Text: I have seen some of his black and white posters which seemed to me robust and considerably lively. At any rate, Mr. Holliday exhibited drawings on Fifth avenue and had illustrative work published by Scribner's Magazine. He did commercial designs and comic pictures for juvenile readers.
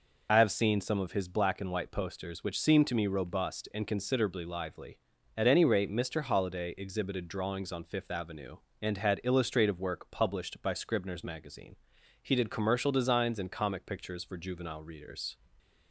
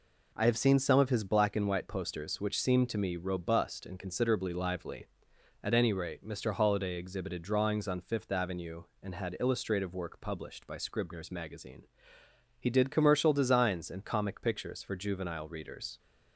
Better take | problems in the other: second | loses the start of "I"; at 0.2 s; 45 ms

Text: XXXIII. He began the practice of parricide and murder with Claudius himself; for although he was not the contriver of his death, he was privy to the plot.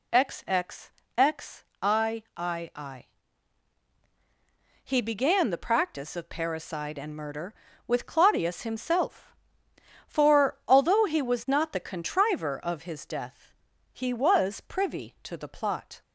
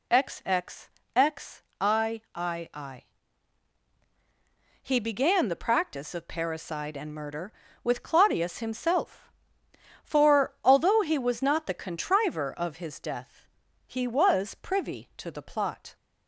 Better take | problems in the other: neither | none

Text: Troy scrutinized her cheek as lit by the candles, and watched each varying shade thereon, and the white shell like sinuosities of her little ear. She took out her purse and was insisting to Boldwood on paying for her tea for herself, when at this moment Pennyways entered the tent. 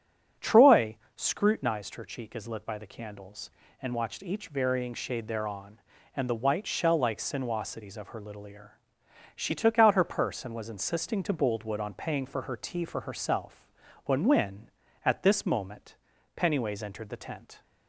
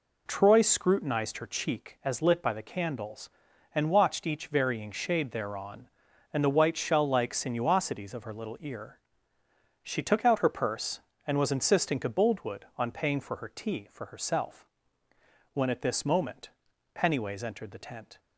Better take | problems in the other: second | starts louder than the rest; strong; until 1.6 s; 7.5 dB // pauses between "Troy" and "scrutinized"; slight; at 0.9 s; 0.20 s long // says "when" twice; at 14.2 s // pauses between "moment" and "Pennyways"; at 15.9 s; 0.40 s long; noticeable in the second

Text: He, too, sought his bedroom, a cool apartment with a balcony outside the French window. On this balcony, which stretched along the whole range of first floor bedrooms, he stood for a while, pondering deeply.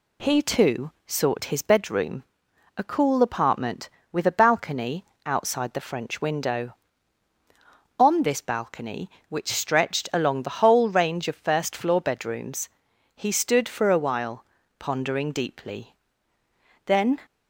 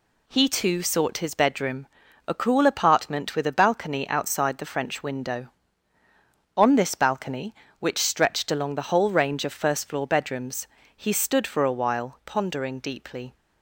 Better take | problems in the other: second | pauses between "balcony" and "outside"; slight; at 5.0 s; 0.18 s long // goes on to say "Then"; slight; from 16.8 s on; 0.34 s long

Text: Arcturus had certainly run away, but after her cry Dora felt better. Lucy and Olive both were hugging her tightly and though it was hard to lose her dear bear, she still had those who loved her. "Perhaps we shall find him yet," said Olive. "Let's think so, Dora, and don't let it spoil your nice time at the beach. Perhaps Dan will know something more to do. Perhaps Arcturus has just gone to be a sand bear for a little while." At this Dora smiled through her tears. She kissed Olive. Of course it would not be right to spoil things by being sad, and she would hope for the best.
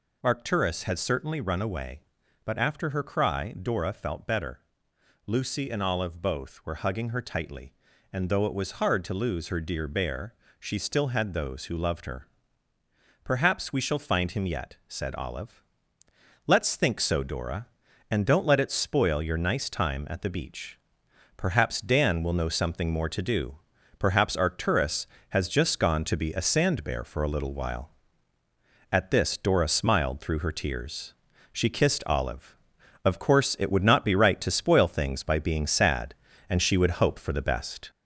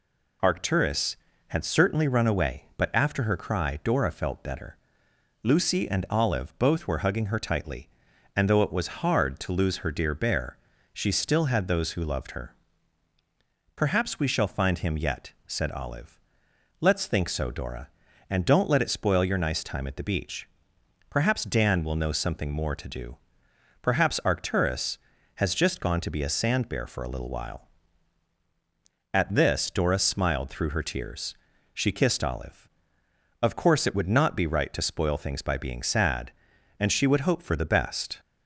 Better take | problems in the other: second | gets louder; throughout; 3.5 dB

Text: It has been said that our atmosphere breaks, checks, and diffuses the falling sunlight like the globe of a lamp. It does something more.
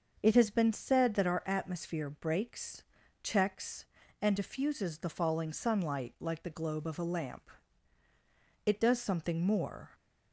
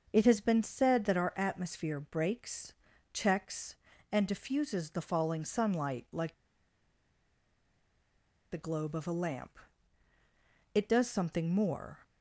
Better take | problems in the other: first | starts louder than the rest; until 1.1 s; 6.5 dB; also in the first // pauses between "like" and "the"; strong; at 6.3 s; 2.1 s long

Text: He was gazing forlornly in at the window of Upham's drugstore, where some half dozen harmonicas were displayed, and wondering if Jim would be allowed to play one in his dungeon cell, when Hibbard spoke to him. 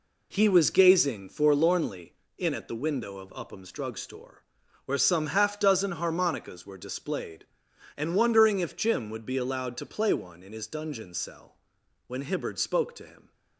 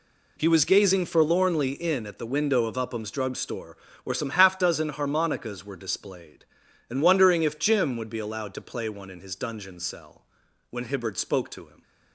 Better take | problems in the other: neither | none

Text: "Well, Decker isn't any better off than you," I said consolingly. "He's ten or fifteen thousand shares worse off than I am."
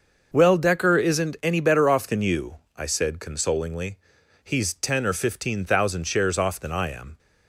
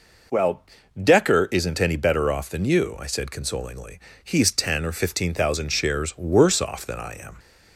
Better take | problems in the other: second | starts louder than the rest; noticeable; until 1.3 s; 6 dB // skips "worse"; at 6.3 s

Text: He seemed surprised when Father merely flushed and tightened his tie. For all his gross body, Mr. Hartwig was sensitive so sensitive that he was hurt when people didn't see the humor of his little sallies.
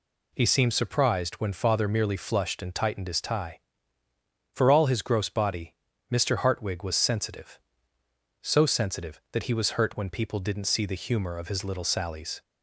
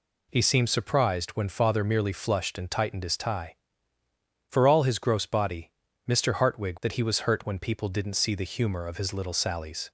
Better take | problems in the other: first | skips "was sensitive so sensitive"; at 6.7 s

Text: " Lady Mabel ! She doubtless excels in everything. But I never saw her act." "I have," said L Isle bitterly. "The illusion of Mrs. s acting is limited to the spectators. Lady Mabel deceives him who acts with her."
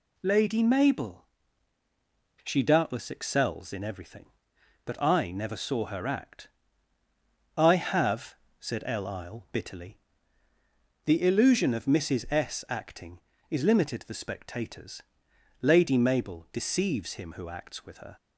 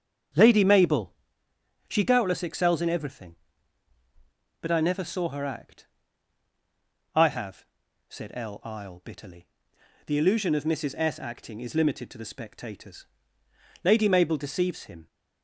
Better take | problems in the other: first | starts louder than the rest; strong; until 2.0 s; 7.5 dB // stops before "who acts with her"; at 15.0 s

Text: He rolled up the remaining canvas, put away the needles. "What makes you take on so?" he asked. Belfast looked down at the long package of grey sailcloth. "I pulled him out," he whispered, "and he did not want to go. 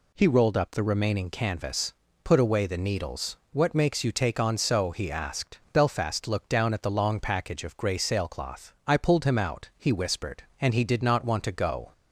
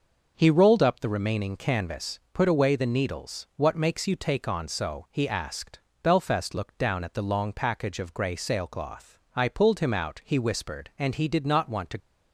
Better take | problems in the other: first | stops before "go"; at 11.9 s

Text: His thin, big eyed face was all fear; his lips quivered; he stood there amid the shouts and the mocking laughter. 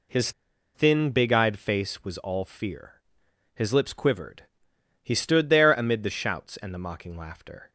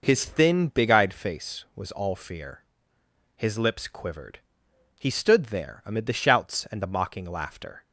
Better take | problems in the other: second | pauses between "His" and "thin"; at 0.3 s; 0.42 s long

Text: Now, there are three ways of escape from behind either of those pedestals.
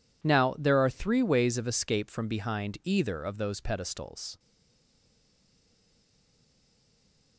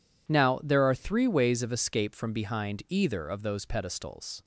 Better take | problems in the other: second | stays silent after the last word; strong; from 4.3 s on; 3.0 s long

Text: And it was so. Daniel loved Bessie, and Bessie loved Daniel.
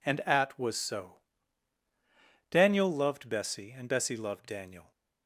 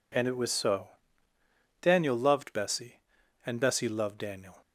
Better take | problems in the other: second | says "at" for "it"; at 0.2 s

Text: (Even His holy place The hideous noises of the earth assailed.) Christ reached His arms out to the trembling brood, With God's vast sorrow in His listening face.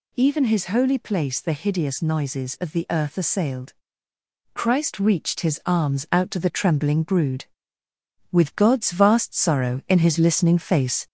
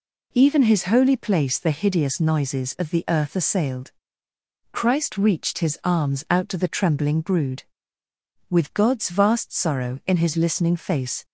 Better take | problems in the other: second | gets louder; slight; throughout; 2.5 dB

